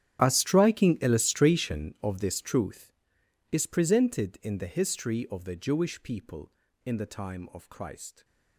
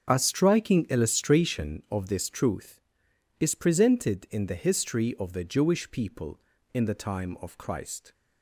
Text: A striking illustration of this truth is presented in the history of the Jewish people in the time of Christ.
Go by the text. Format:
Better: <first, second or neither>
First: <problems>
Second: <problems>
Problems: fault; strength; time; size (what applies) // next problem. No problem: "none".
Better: second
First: gets quieter; strong; throughout; 19 dB // starts louder than the rest; strong; until 1.2 s; 9.5 dB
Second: starts louder than the rest; until 1.1 s; 6.5 dB